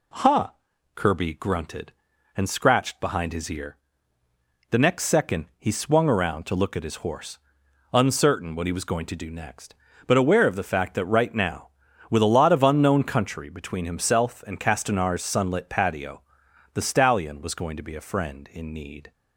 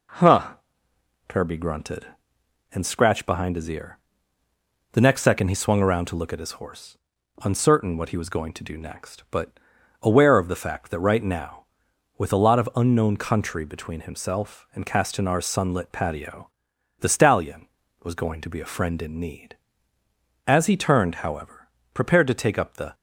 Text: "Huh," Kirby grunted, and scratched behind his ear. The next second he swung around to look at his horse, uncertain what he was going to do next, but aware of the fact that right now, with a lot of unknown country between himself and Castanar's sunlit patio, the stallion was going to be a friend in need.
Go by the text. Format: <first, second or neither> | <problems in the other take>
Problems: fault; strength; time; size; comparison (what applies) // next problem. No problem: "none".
first | pauses between "but" and "aware"; at 9.5 s; 0.44 s long // goes on to say "As he turned however prepared to take up the"; strong; from 20.4 s on; 2.4 s long